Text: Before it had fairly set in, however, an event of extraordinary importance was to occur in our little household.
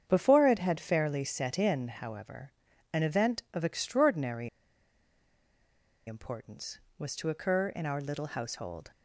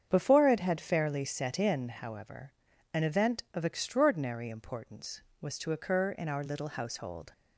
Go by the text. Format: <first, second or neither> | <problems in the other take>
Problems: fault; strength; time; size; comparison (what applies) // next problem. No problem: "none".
second | starts louder than the rest; strong; until 1.0 s; 7.5 dB; strong in the second // pauses between "extraordinary" and "importance"; strong; at 4.4 s; 1.5 s long